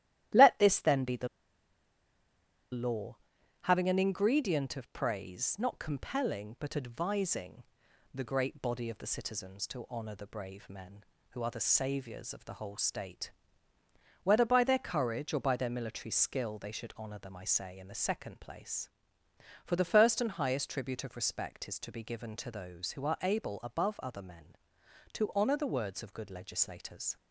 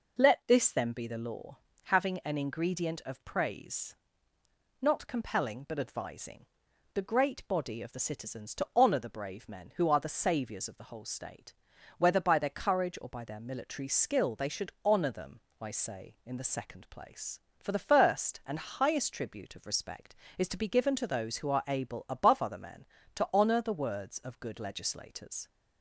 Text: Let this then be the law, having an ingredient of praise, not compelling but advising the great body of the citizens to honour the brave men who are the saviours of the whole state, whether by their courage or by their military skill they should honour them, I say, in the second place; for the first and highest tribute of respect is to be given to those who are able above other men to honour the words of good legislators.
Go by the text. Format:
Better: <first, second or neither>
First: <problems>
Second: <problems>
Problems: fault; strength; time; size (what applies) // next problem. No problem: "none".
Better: second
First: starts louder than the rest; strong; until 2.8 s; 13 dB // pauses between "the" and "law"; strong; at 1.2 s; 1.4 s long // pauses between "advising" and "the"; noticeable; at 7.6 s; 0.52 s long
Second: pauses between "advising" and "the"; noticeable; at 6.4 s; 0.48 s long